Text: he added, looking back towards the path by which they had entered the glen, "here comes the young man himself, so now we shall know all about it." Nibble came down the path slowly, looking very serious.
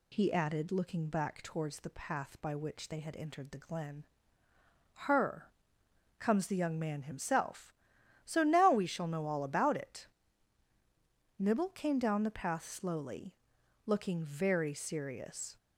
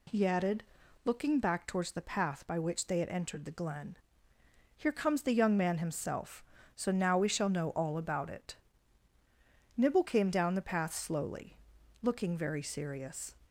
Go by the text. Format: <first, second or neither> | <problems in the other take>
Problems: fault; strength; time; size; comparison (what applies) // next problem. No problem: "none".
second | says "her" for "here"; at 5.0 s